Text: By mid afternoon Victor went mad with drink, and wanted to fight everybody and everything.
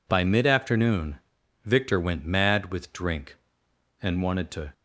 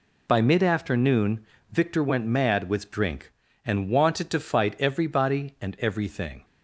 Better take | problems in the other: second | pauses between "afternoon" and "Victor"; noticeable; at 1.1 s; 0.46 s long; slight in the second // stops before "fight everybody and everything"; at 4.7 s

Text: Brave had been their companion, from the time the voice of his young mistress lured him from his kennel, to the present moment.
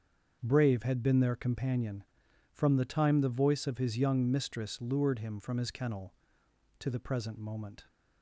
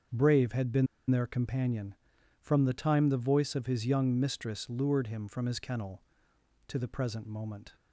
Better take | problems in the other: first | starts louder than the rest; until 1.3 s; 7 dB; also in the first // pauses between "been" and "their"; slight; at 0.8 s; 0.23 s long

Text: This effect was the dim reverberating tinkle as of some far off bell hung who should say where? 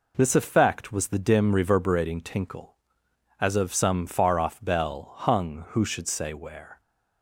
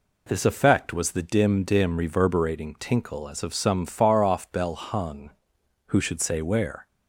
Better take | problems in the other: first | says "dim" twice; at 1.6 s

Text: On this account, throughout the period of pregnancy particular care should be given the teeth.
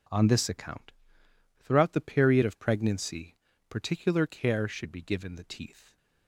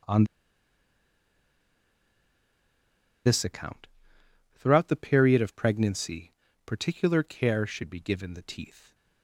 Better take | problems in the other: first | pauses between "On" and "this"; strong; at 0.2 s; 3.0 s long // pauses between "pregnancy" and "particular"; slight; at 6.3 s; 0.34 s long; slight in the first

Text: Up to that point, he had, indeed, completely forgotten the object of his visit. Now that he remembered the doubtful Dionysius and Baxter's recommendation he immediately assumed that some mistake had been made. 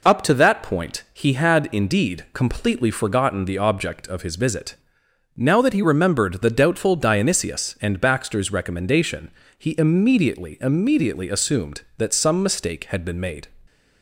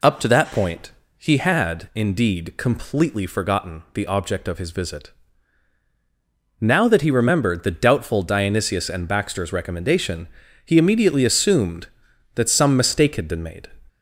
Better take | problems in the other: second | pauses between "recommendation" and "he"; slight; at 9.3 s; 0.26 s long; slight in the second // says "immediately" twice; at 10.5 s

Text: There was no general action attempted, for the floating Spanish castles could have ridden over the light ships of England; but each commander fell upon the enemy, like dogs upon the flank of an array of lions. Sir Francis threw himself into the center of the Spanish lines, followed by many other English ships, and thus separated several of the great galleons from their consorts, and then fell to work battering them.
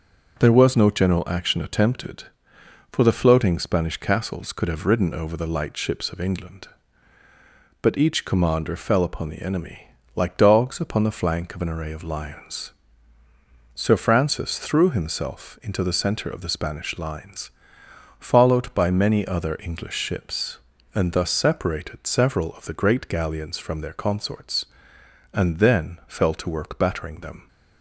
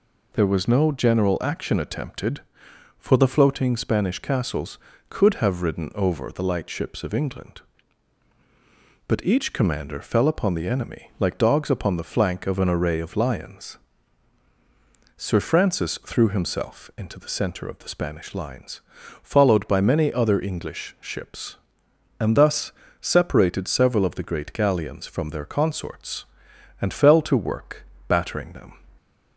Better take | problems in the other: first | pauses between "thus" and "separated"; slight; at 22.7 s; 0.30 s long // skips "then"; at 26.9 s // pauses between "work" and "battering"; slight; at 27.8 s; 0.24 s long

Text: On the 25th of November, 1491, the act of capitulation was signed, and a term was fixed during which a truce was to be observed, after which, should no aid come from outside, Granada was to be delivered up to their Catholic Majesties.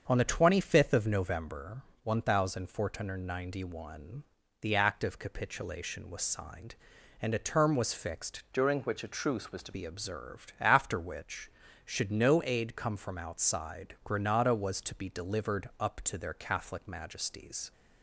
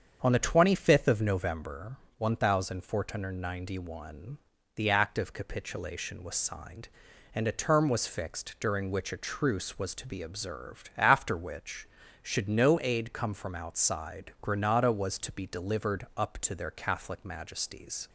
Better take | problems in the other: second | starts louder than the rest; until 1.0 s; 7 dB; strong in the second // changes voice from "during" to "to"; from 8.5 to 9.7 s; 1.2 s long

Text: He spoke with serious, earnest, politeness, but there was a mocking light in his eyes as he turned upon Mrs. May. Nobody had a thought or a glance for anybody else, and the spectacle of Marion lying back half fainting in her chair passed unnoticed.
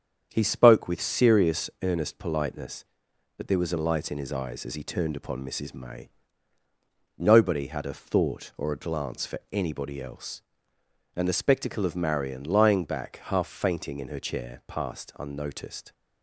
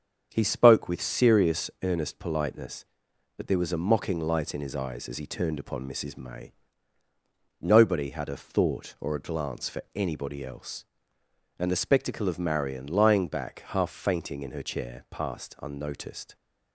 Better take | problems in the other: second | starts louder than the rest; strong; until 1.3 s; 8 dB; strong in the second // skips "mocking"; at 3.7 s

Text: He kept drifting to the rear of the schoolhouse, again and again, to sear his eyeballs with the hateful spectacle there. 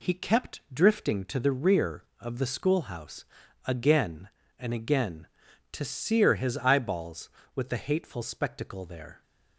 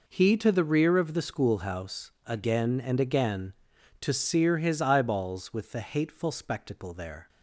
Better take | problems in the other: first | skips "kept drifting"; at 0.3 s

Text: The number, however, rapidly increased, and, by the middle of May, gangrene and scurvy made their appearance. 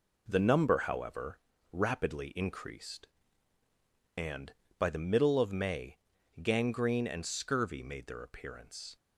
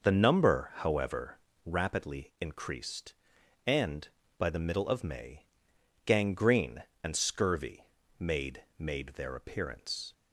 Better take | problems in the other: first | pauses between "scurvy" and "made"; slight; at 7.8 s; 0.32 s long // says "made" twice; at 8.7 s

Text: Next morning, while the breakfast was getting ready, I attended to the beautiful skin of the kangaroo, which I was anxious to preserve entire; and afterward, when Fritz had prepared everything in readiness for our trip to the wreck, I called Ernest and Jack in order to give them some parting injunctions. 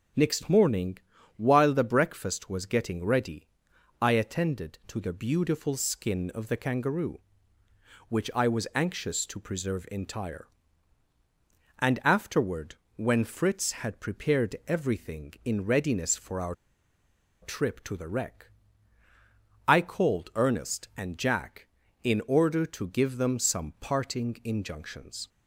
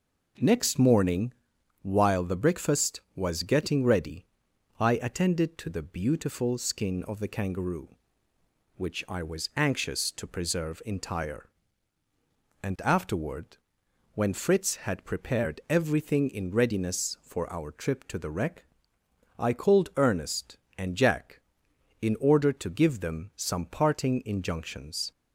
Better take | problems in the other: second | starts louder than the rest; noticeable; until 1.5 s; 6 dB // pauses between "our" and "trip"; noticeable; at 16.5 s; 0.88 s long

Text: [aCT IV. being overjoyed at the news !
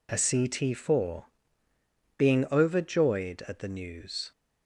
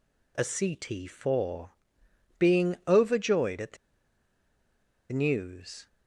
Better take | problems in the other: first | pauses between "the" and "news"; strong; at 3.7 s; 1.3 s long

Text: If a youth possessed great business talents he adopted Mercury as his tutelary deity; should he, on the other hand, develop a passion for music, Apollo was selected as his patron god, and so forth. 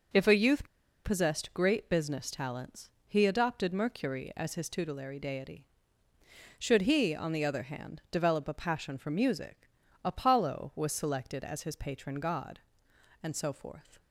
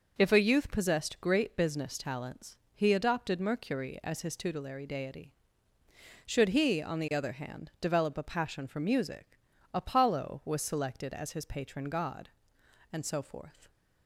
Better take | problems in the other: second | pauses between "youth" and "possessed"; at 0.6 s; 0.38 s long // pauses between "talents" and "he"; slight; at 2.8 s; 0.16 s long; slight in the second

